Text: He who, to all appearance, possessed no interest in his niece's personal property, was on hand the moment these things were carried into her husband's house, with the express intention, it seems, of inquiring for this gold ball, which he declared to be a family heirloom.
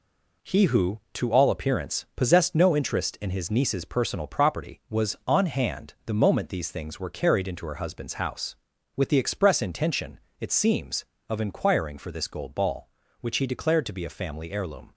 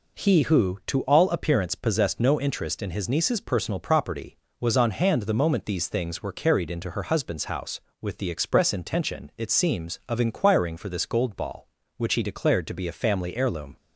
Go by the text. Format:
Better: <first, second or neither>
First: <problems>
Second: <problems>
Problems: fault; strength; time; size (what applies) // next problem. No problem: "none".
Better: second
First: gets quieter; throughout; 6.5 dB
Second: none